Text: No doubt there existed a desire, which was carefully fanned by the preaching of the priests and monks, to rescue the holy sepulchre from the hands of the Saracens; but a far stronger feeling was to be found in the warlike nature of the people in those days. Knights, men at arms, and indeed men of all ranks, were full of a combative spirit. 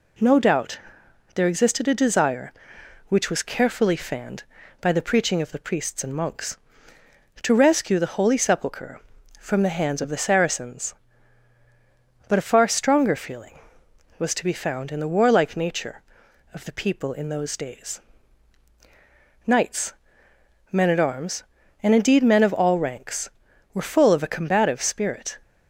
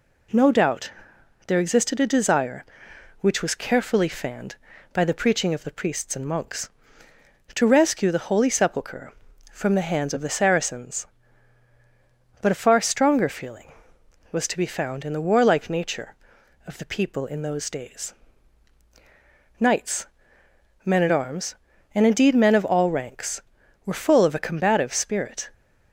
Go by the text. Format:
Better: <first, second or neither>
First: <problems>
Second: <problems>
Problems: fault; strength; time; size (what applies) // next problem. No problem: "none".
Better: neither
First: pauses between "doubt" and "there"; noticeable; at 0.7 s; 0.54 s long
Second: pauses between "doubt" and "there"; noticeable; at 0.9 s; 0.54 s long